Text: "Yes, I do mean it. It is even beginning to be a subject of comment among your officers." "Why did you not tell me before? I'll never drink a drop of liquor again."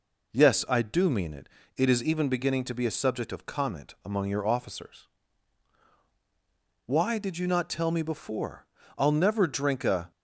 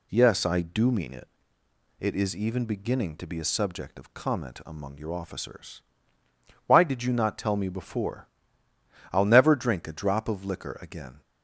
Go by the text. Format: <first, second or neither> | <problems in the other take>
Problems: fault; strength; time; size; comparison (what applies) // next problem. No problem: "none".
second | stops before "drop of liquor again"; at 10.1 s